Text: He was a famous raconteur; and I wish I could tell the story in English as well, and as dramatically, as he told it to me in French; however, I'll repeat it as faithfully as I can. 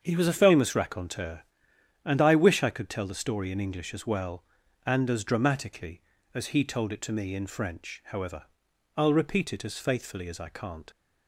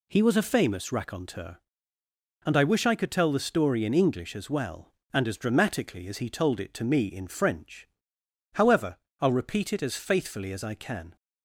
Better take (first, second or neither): second